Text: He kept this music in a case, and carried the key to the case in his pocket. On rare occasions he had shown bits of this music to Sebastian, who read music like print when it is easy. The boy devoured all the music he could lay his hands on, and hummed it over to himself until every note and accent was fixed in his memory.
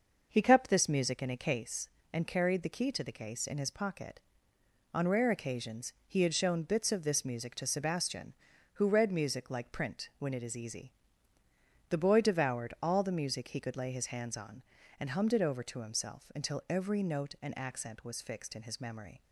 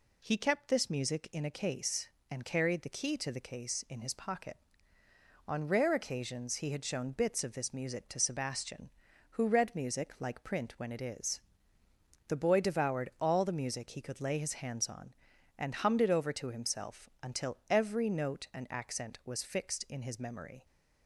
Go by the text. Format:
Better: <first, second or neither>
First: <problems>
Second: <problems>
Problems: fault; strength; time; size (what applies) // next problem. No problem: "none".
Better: first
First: none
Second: skips "easy"; at 11.8 s